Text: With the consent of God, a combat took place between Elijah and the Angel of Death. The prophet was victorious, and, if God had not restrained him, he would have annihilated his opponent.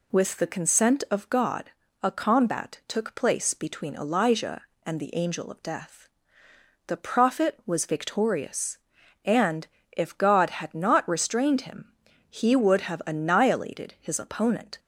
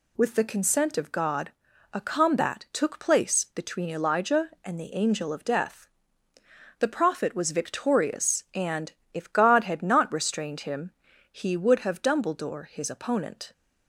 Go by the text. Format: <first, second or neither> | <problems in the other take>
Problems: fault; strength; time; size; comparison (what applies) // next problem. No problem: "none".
first | says "dumbledore" for "annihilated"; at 12.0 s